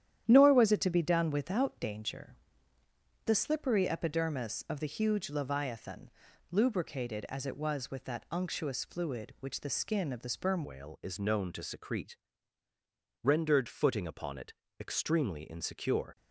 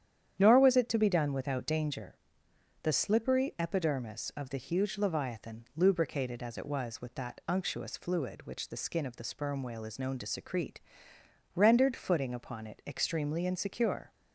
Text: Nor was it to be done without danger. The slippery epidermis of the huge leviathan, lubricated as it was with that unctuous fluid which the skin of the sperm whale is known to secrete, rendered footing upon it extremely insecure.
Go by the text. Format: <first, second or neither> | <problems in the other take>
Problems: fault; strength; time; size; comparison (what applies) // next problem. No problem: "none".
second | starts louder than the rest; strong; until 1.2 s; 10.5 dB; strong in the second // changes voice at "whale"; from 10.6 s on; 5.5 s long // pauses between "it" and "extremely"; slight; at 14.5 s; 0.26 s long